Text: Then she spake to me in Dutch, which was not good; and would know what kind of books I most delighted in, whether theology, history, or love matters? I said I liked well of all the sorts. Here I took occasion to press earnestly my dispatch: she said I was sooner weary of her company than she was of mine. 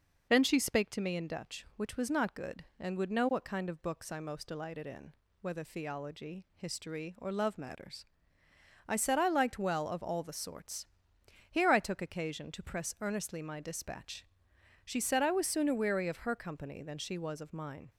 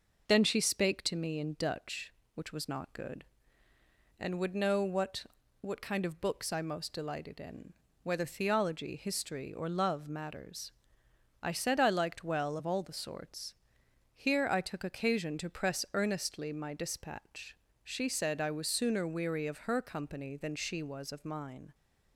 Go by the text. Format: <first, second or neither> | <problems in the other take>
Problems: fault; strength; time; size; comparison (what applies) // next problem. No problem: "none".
first | says "what" twice; at 5.6 s